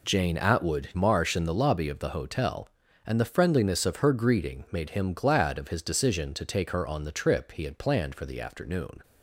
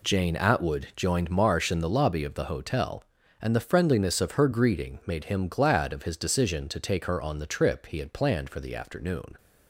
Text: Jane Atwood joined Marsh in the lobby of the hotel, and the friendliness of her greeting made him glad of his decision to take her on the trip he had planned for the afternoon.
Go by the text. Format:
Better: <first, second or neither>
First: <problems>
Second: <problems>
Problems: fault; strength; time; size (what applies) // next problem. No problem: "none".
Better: second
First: skips "joined"; at 0.9 s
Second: none